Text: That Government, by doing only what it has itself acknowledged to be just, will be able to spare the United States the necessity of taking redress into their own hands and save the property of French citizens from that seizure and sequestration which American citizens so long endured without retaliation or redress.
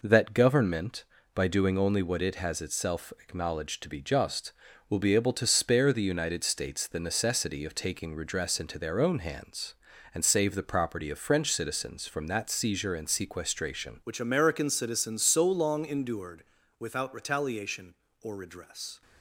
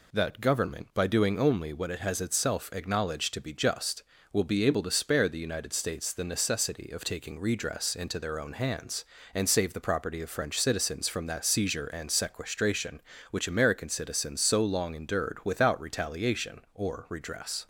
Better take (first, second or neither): second